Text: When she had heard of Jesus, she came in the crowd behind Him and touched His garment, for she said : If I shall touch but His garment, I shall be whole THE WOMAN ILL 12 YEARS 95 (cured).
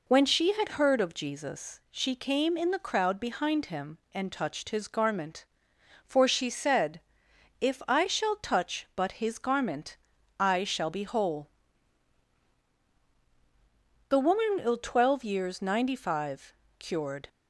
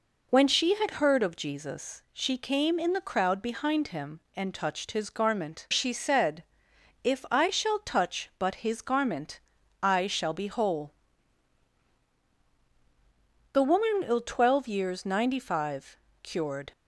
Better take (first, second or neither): first